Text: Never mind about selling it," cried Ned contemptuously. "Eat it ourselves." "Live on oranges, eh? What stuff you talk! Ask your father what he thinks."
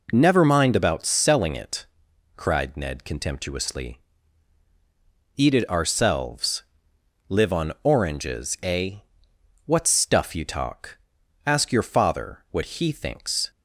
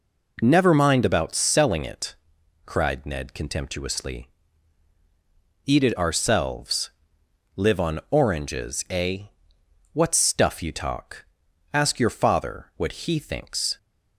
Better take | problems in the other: neither | none

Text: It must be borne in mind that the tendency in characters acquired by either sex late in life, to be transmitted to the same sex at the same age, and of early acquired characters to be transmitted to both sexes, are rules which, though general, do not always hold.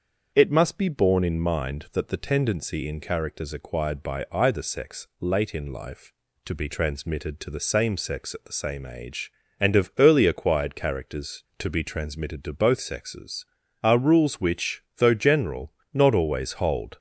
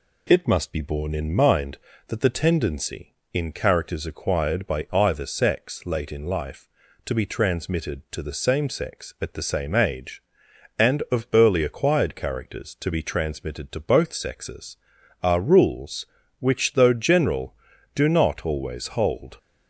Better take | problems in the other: second | starts louder than the rest; until 1.3 s; 7 dB // skips "do"; at 15.8 s

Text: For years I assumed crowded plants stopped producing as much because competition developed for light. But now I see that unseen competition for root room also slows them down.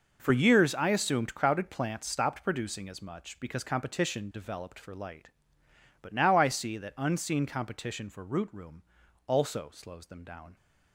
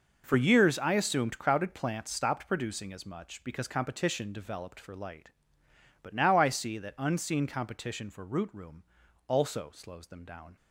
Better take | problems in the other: neither | pauses between "room" and "also"; the same in both

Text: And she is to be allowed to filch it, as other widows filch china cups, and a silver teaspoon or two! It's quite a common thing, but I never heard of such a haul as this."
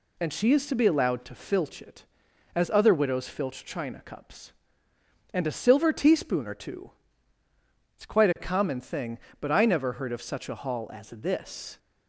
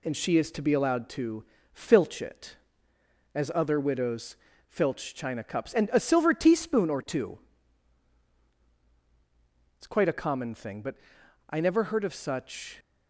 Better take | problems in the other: first | pauses between "to" and "filch"; slight; at 1.4 s; 0.28 s long // pauses between "widows" and "filch"; slight; at 4.3 s; 0.32 s long // pauses between "but" and "I"; noticeable; at 10.9 s; 0.54 s long // stops before "a haul as this"; at 12.7 s

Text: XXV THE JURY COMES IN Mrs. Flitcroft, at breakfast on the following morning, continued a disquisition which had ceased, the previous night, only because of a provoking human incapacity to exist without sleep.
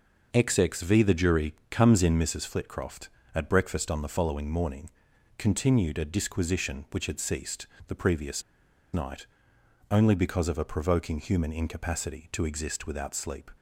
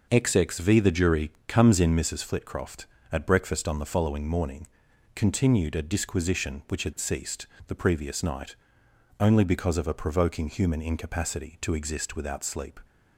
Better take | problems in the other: second | pauses between "JURY" and "COMES"; slight; at 1.5 s; 0.16 s long; slight in the second // pauses between "previous" and "night"; noticeable; at 8.4 s; 0.52 s long

